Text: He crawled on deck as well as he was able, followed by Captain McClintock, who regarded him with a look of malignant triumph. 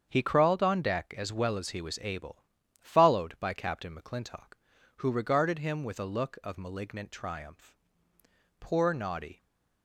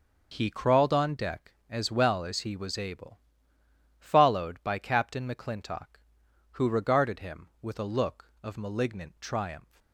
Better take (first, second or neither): second